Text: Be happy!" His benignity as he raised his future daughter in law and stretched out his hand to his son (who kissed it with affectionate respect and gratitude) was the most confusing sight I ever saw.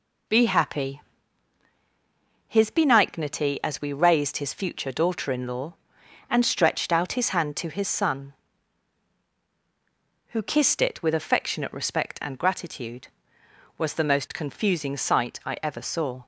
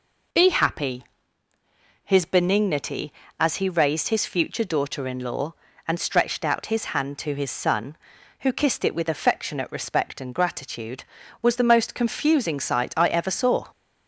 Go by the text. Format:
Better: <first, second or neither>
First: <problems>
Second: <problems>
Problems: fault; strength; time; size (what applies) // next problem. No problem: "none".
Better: second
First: says "we" for "he"; at 3.8 s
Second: none